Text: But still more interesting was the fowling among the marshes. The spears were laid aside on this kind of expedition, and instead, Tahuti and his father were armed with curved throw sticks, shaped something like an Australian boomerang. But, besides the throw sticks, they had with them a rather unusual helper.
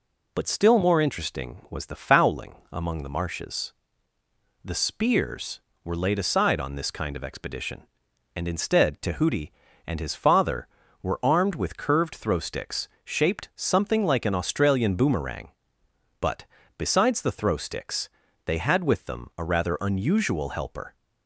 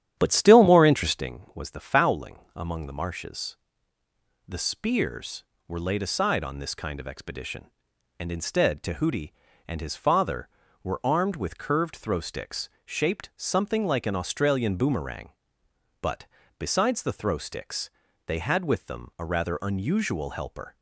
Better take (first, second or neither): first